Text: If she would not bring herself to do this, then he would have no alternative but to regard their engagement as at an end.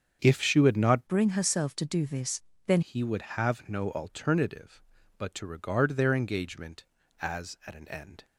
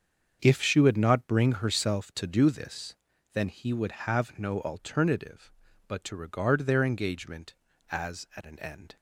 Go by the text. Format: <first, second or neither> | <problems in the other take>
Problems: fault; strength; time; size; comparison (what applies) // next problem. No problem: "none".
second | starts louder than the rest; strong; until 1.2 s; 7.5 dB; also in the second // changes voice from "bring" to "then"; from 1.0 to 2.8 s; 1.8 s long